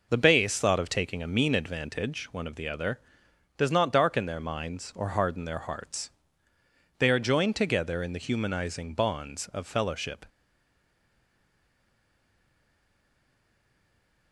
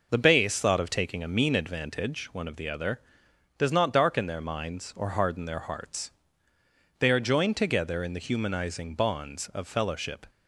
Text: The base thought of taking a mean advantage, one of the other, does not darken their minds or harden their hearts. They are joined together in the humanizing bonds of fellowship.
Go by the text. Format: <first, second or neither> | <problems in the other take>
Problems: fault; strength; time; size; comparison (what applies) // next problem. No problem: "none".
second | stays silent after the last word; strong; from 10.2 s on; 4.1 s long